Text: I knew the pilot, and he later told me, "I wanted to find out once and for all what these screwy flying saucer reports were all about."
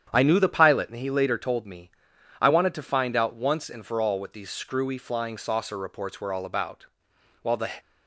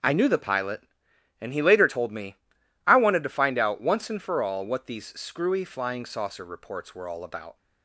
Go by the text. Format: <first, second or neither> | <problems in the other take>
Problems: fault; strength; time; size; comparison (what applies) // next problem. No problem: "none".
second | starts louder than the rest; strong; until 1.1 s; 9 dB; also in the second // goes on to say "While the"; slight; from 7.4 s on; 0.30 s long